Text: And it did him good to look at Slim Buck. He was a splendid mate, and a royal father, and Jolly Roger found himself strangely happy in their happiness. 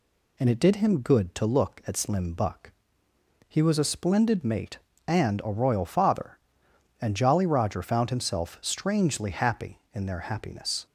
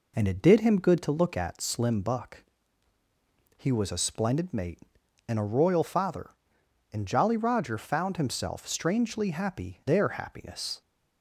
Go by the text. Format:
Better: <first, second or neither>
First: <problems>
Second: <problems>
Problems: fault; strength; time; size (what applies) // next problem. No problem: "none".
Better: first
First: none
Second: skips "in"; at 9.8 s